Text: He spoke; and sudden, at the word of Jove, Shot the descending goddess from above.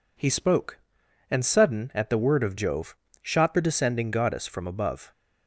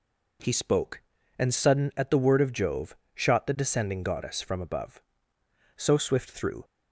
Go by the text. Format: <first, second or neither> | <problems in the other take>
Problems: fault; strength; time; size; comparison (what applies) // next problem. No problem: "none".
first | goes on to say "So swift through"; noticeable; from 5.7 s on; 0.88 s long